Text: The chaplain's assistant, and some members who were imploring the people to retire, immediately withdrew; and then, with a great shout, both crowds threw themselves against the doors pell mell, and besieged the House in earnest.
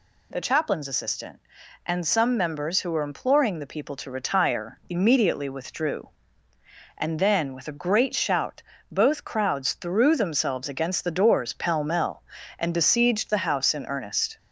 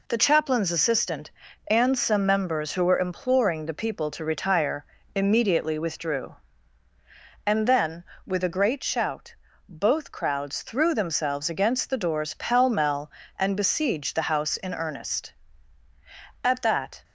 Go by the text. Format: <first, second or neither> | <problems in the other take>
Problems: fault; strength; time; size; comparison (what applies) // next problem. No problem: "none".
first | goes on to say "At that"; from 16.4 s on; 0.60 s long